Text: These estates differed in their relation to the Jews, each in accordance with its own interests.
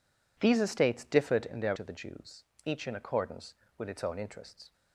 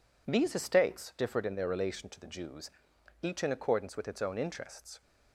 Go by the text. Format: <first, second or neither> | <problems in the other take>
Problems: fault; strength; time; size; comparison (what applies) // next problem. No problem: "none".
second | skips "relation"; at 1.7 s